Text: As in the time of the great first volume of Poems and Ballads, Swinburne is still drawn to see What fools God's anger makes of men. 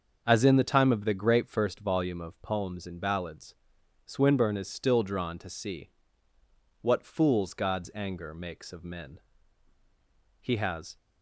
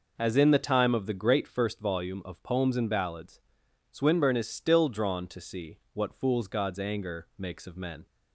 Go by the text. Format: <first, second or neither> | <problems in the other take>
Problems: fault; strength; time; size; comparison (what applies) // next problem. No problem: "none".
second | starts louder than the rest; until 1.2 s; 6.5 dB // pauses between "see" and "What"; noticeable; at 5.9 s; 0.90 s long // goes on to say "He has"; from 10.4 s on; 0.56 s long